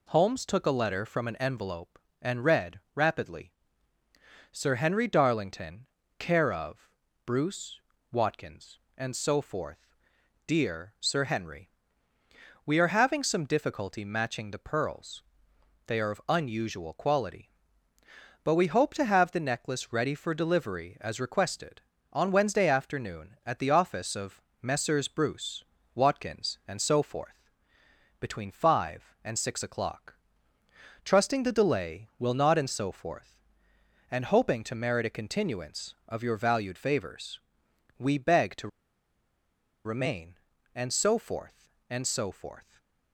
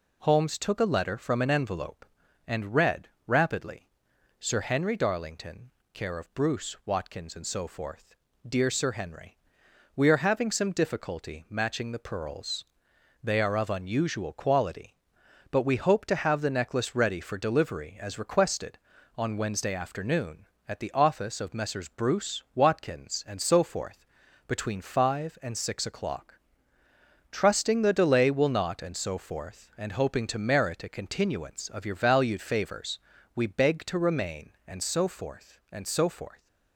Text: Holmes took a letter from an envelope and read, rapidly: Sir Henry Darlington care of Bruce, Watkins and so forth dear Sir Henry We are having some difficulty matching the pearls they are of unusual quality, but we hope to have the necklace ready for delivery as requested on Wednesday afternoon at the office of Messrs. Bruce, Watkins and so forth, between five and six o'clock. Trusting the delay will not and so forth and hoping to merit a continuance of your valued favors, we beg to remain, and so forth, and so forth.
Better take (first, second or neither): second